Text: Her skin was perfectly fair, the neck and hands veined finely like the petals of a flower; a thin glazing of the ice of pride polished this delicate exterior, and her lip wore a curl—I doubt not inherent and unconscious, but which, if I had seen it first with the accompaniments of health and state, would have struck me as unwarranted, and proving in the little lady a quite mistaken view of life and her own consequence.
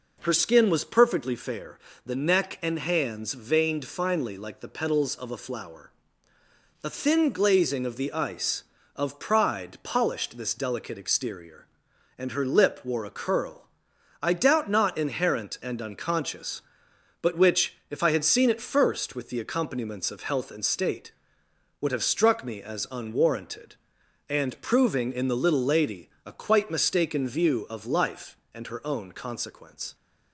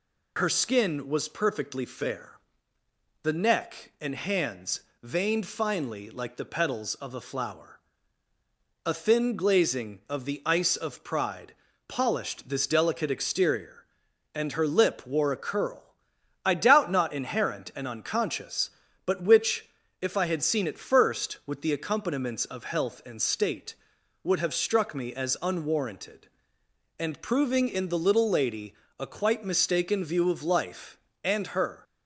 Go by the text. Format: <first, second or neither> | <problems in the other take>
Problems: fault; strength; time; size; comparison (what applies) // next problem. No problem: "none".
first | pauses between "hands" and "veined"; slight; at 4.8 s; 0.20 s long // pauses between "pride" and "polished"; slight; at 11.5 s; 0.32 s long // pauses between "lady" and "a"; slight; at 28.7 s; 0.24 s long; slight in the first // stops before "own consequence"; at 31.8 s